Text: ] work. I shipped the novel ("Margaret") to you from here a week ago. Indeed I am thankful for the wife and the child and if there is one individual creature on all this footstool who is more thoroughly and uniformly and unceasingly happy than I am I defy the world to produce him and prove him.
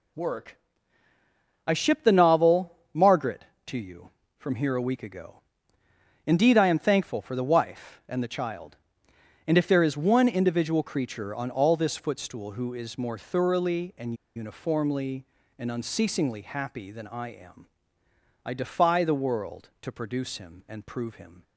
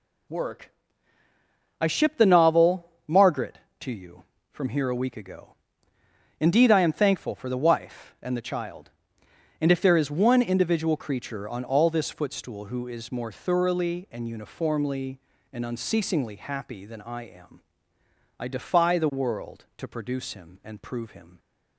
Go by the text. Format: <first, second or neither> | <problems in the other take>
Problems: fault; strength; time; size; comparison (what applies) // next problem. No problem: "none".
second | pauses between "and" and "uniformly"; slight; at 14.1 s; 0.21 s long // pauses between "am" and "I"; noticeable; at 17.6 s; 0.78 s long; noticeable in the second